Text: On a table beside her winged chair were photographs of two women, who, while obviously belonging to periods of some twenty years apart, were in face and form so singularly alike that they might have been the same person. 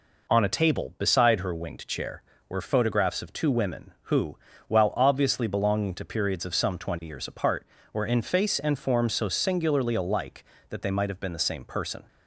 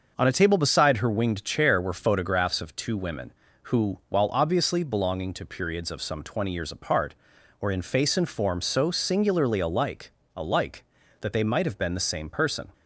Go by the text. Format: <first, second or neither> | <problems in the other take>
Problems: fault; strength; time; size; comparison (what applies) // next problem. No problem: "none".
first | starts louder than the rest; until 1.1 s; 6 dB // says "alike" twice; at 10.3 s